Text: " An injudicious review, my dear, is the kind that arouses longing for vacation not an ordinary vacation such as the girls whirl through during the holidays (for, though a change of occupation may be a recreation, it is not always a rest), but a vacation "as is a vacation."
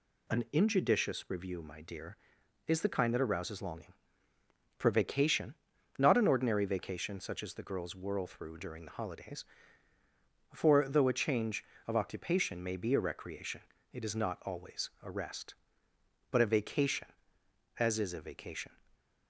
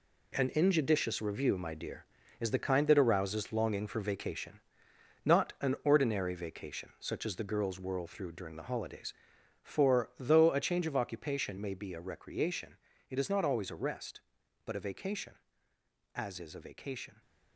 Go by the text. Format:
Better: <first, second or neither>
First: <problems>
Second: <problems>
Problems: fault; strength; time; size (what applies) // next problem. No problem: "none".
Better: first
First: pauses between "vacation" and "not"; at 5.5 s; 0.44 s long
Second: gets quieter; strong; throughout; 9.5 dB // pauses between "vacation" and "not"; noticeable; at 4.6 s; 0.62 s long